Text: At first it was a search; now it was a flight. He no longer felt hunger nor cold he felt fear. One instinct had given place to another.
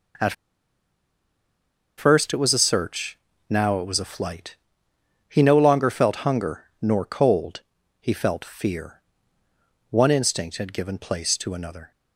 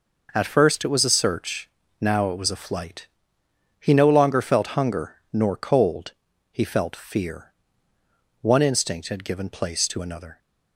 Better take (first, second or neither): second